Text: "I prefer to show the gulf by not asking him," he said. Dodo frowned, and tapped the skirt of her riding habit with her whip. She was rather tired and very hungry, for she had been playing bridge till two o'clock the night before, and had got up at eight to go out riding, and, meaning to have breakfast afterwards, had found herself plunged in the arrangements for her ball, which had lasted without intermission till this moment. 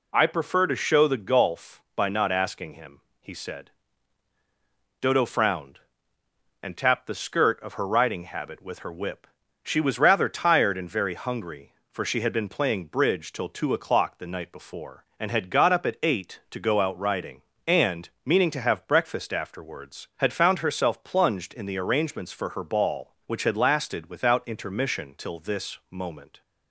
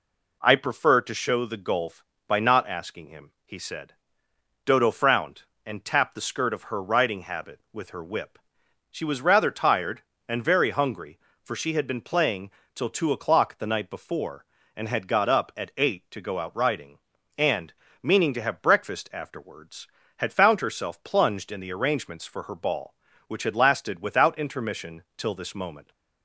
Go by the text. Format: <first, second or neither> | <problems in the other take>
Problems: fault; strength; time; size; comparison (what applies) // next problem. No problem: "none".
first | skips "bridge"; at 12.6 s